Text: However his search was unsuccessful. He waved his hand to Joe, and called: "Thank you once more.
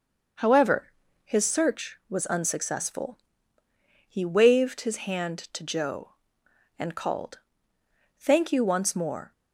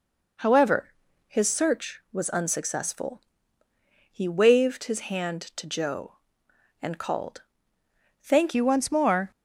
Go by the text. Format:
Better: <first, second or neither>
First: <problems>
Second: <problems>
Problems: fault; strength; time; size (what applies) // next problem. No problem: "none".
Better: first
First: pauses between "However" and "his"; slight; at 0.9 s; 0.34 s long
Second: pauses between "However" and "his"; slight; at 0.9 s; 0.36 s long // changes voice at "you"; from 8.5 s on; 0.8 s long